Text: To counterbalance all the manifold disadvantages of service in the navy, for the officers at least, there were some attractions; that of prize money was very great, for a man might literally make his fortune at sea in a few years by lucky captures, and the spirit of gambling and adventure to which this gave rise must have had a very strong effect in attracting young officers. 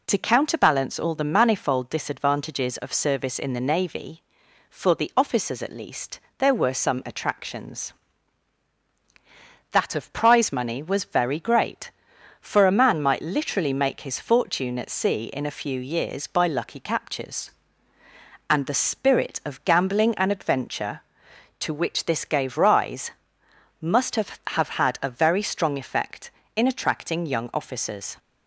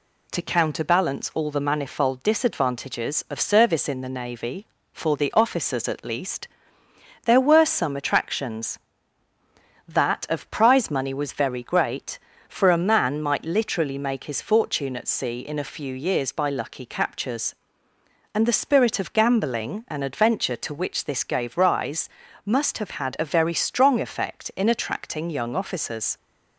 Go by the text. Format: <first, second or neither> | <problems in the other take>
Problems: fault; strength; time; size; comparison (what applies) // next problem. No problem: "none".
second | pauses between "rise" and "must"; noticeable; at 23.1 s; 0.70 s long; slight in the second // says "have" twice; at 24.4 s